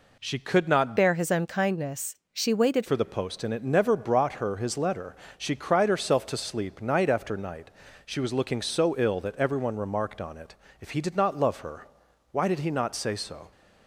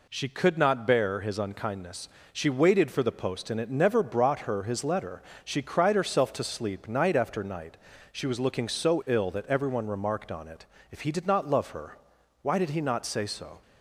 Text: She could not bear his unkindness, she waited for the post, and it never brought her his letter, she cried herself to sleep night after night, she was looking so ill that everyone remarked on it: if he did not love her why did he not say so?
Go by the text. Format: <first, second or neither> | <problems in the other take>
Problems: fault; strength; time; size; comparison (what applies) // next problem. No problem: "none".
second | changes voice from "bear" to "waited"; from 0.9 to 2.8 s; 1.9 s long // pauses between "her" and "why"; noticeable; at 11.8 s; 0.46 s long; noticeable in the second